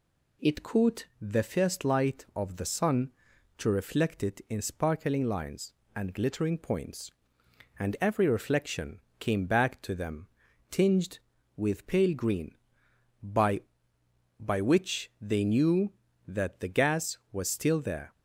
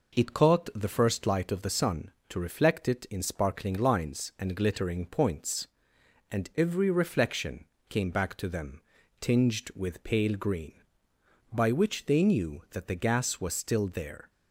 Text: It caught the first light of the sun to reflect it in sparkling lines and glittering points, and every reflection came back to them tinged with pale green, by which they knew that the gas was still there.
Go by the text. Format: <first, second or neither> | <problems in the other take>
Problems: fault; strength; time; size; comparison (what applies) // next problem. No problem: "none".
second | pauses between "reflection" and "came"; slight; at 8.9 s; 0.18 s long; slight in the second // pauses between "them" and "tinged"; at 10.2 s; 0.42 s long; also in the second // says "by" twice; at 14.3 s